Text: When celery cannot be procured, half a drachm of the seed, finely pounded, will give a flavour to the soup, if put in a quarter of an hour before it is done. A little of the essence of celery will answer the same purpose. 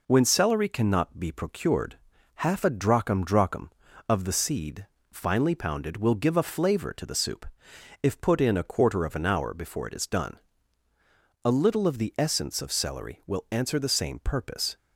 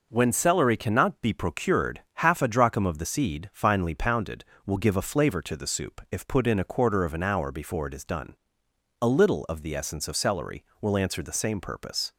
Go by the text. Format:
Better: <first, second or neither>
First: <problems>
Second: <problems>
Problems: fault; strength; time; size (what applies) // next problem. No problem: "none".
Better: second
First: says "drachm" twice; at 3.2 s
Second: none